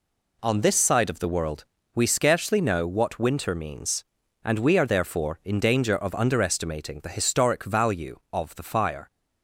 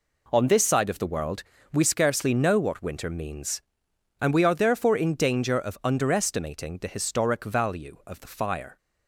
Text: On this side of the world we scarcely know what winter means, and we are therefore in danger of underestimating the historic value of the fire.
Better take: neither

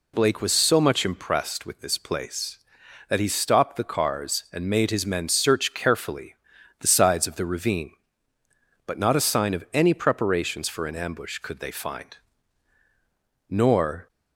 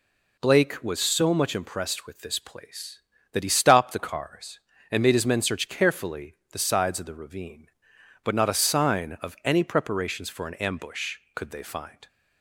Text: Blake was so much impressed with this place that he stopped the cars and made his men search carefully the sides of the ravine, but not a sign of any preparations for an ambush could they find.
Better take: second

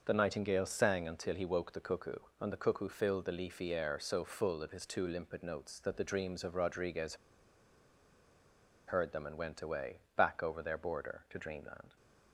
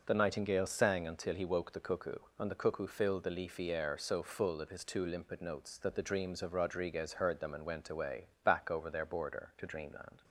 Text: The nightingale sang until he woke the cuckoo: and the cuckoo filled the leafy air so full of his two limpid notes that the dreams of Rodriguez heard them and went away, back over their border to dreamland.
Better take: second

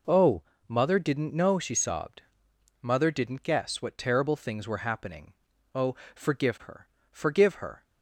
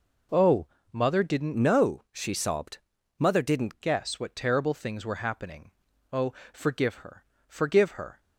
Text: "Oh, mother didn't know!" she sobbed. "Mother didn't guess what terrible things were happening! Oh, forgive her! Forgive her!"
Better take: first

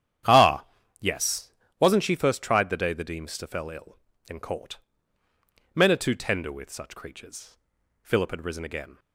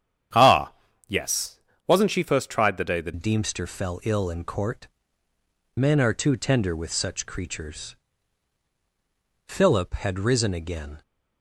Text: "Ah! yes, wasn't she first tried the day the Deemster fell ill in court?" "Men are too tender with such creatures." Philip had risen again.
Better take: first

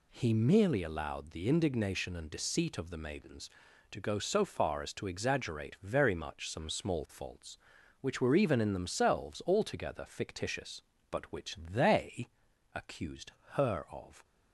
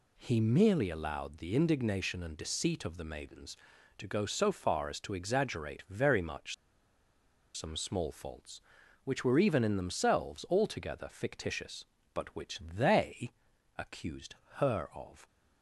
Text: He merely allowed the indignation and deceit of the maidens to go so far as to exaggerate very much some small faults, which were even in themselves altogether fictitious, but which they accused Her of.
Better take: first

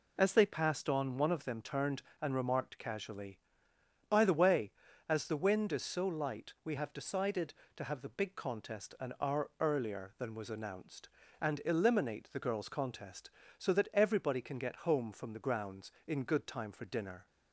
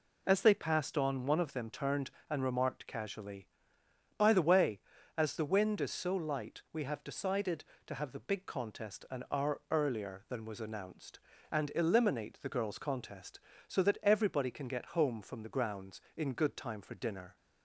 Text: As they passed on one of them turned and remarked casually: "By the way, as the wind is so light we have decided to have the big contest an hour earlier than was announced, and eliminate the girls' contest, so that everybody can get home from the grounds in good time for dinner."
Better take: neither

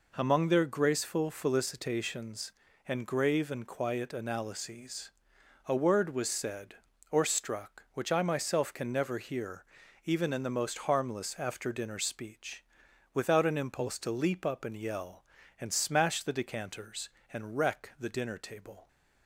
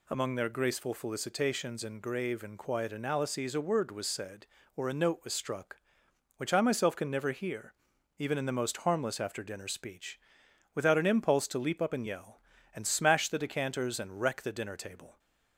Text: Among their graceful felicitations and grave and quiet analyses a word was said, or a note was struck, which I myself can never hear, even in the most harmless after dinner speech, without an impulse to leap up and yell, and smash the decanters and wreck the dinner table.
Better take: second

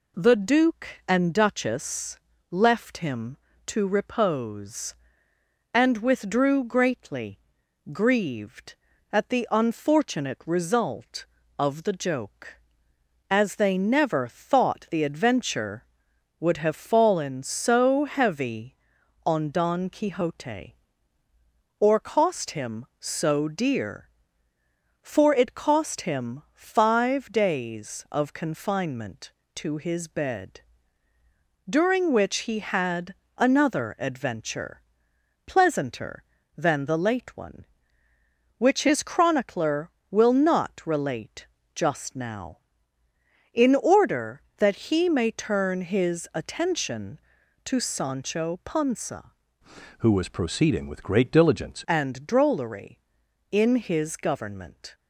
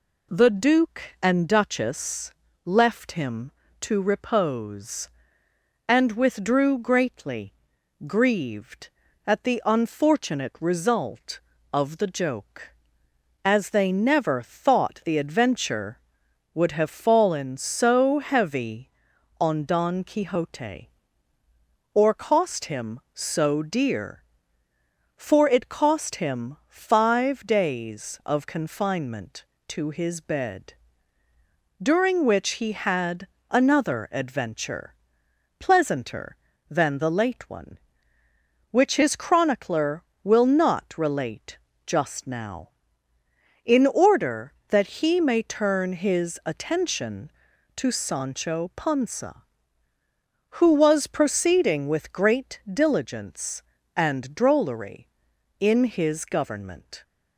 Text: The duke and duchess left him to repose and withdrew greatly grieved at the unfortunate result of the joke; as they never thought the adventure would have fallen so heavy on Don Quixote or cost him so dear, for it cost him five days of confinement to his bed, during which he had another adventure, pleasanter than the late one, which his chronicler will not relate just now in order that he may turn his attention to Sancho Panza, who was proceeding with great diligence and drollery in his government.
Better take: second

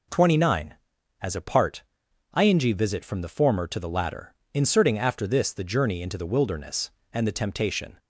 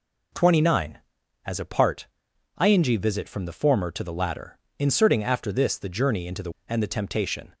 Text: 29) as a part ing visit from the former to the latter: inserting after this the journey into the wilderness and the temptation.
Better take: first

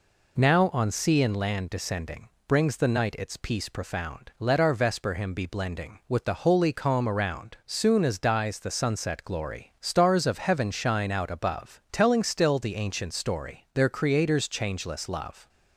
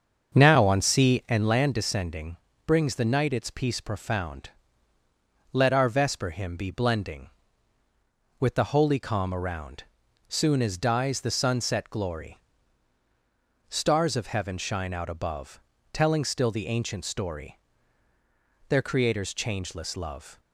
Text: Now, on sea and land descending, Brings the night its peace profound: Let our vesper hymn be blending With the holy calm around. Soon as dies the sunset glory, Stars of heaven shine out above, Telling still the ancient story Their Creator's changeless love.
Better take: first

